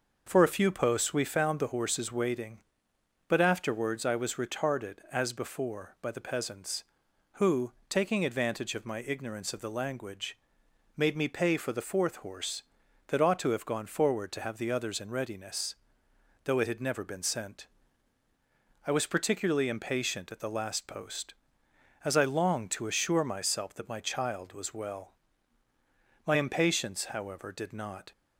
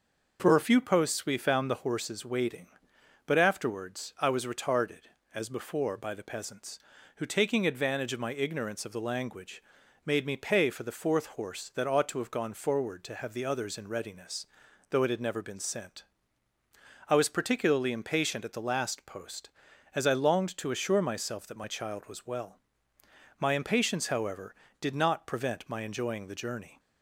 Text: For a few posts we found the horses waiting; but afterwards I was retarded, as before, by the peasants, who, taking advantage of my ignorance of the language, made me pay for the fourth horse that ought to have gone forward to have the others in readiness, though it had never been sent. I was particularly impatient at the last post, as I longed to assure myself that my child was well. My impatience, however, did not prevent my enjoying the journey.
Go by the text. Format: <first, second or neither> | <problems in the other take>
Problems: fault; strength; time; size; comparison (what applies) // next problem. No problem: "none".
second | starts louder than the rest; noticeable; until 1.2 s; 6 dB // stops before "prevent my enjoying the journey"; at 28.1 s